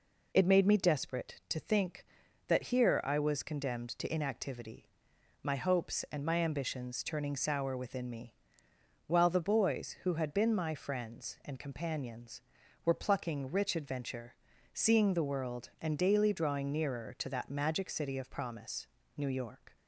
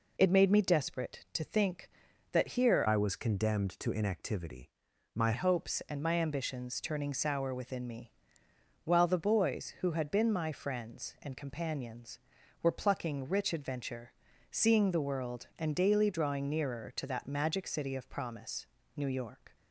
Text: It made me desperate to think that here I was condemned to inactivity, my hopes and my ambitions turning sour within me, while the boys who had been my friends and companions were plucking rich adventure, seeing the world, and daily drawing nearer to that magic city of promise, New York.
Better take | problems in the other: first | changes voice from "I" to "my"; from 2.8 to 5.3 s; 2.5 s long

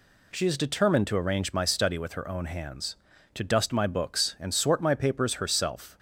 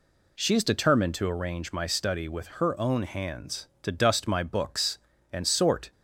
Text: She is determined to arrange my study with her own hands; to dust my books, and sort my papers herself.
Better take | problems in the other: first | stops before "my papers herself"; at 5.9 s

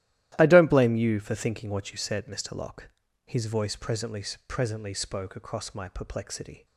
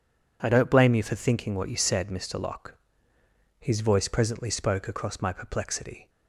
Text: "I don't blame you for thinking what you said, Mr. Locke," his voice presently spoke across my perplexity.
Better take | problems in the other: second | starts louder than the rest; strong; until 1.3 s; 14 dB // says "presently" twice; at 4.4 s

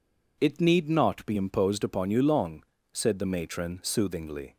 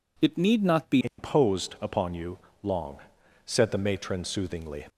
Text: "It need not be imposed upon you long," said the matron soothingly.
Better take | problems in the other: first | changes voice at "imposed"; from 1.0 s on; 3.8 s long // pauses between "you" and "long"; slight; at 2.3 s; 0.24 s long

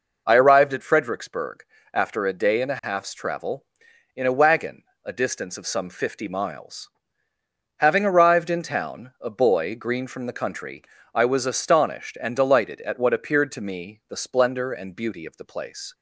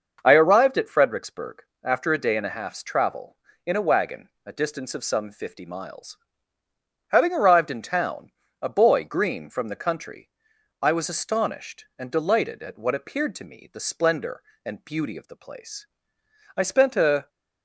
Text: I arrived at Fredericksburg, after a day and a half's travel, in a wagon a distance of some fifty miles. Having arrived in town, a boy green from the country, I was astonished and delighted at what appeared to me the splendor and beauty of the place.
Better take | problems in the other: first | starts louder than the rest; until 1.2 s; 6.5 dB // pauses between "wagon" and "a"; slight; at 4.2 s; 0.16 s long; slight in the first // goes on to say "I spent a"; noticeable; from 16.5 s on; 0.72 s long

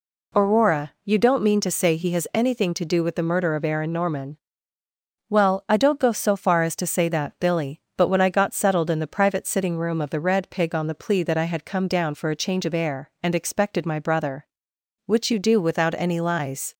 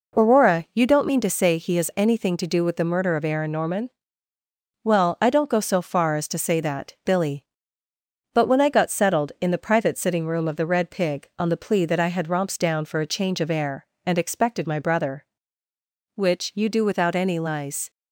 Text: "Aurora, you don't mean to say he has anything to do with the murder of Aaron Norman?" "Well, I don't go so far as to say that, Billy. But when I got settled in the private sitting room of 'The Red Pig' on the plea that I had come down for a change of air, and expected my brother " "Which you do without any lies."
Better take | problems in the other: first | says "romps" for "come"; at 12.2 s

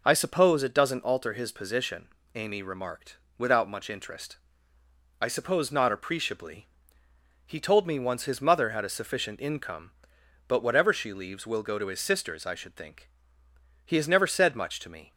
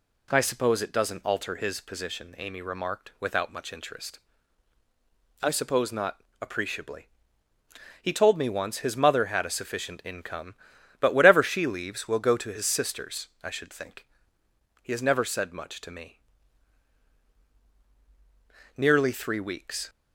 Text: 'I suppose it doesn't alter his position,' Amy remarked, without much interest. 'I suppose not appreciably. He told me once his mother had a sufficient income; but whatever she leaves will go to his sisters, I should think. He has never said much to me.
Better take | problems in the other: first | pauses between "not" and "appreciably"; slight; at 6.2 s; 0.20 s long // goes on to say "Nearly three weeks"; noticeable; from 18.7 s on; 1.1 s long

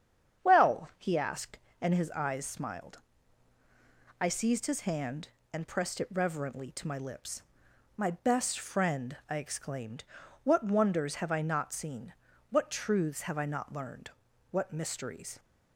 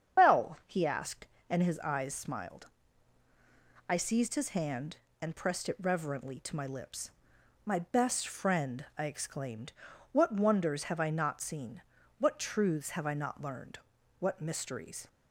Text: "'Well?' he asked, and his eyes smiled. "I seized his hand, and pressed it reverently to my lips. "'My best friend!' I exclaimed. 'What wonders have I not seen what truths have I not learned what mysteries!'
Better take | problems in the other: first | loses the start of "Well"; at 0.1 s; 80 ms // starts louder than the rest; strong; until 1.2 s; 7.5 dB; strong in the first // pauses between "seen" and "what"; at 11.8 s; 0.38 s long; also in the first // pauses between "learned" and "what"; at 13.7 s; 0.40 s long; also in the first

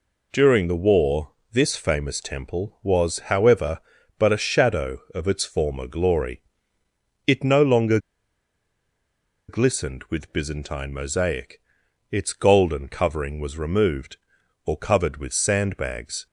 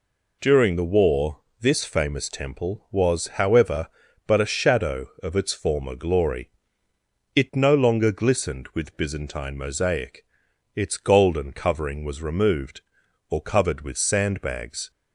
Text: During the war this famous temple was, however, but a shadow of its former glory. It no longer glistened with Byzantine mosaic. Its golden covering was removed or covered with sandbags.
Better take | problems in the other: second | pauses between "war" and "this"; slight; at 1.3 s; 0.20 s long; slight in the second // pauses between "longer" and "glistened"; strong; at 7.9 s; 1.5 s long

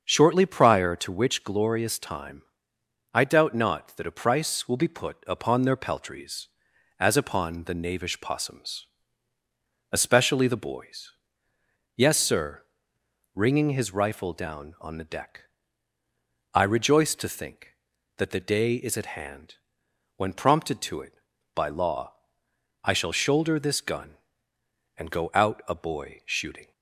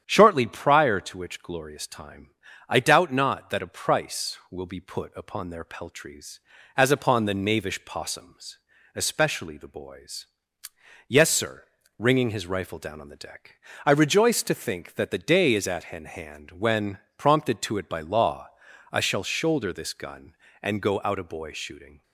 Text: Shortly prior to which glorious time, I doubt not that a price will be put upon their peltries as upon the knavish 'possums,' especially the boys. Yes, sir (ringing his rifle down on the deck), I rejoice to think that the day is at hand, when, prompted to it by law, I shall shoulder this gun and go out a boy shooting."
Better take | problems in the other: first | starts louder than the rest; strong; until 1.0 s; 9 dB; also in the first // says "hand" twice; at 16.0 s

